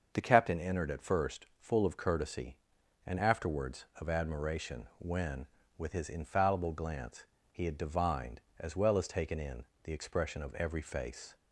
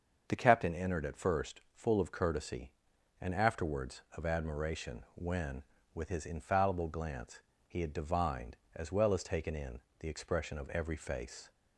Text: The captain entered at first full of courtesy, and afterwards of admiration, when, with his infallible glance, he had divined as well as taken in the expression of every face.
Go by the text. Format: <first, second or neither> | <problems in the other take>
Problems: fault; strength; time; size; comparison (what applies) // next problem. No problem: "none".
neither | starts louder than the rest; the same in both // pauses between "first" and "full"; slight; the same in both // pauses between "in" and "the"; slight; the same in both